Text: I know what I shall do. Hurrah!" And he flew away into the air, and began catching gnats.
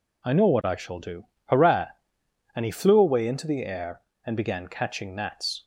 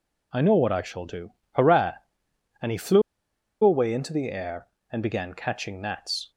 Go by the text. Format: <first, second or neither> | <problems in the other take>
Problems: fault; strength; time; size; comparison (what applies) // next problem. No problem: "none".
first | pauses between "flew" and "away"; noticeable; at 3.0 s; 0.62 s long